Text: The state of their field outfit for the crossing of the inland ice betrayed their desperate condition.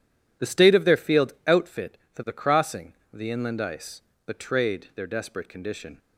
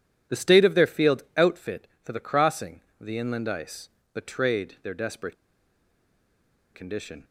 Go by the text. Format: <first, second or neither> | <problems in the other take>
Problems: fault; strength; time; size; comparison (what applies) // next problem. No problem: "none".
first | pauses between "ice" and "betrayed"; slight; at 3.8 s; 0.24 s long; slight in the first // pauses between "desperate" and "condition"; strong; at 5.3 s; 1.4 s long